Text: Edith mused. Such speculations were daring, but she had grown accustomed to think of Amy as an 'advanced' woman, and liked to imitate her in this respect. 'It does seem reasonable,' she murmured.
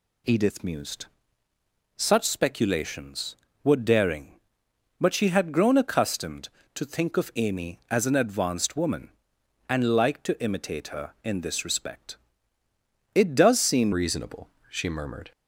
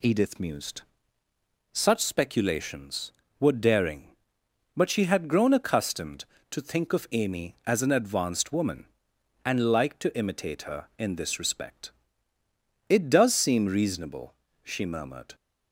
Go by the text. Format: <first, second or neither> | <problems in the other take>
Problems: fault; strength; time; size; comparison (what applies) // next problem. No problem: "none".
second | changes voice at "reasonable"; from 13.9 s on; 1.4 s long